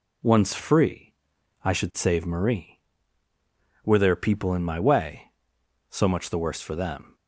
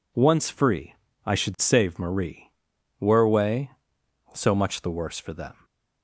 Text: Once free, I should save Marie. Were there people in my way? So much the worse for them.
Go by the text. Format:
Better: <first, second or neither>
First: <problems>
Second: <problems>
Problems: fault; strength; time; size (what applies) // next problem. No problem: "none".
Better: first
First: none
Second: skips "there people in my"; at 3.2 s // stays silent after the last word; slight; from 5.5 s on; 0.5 s long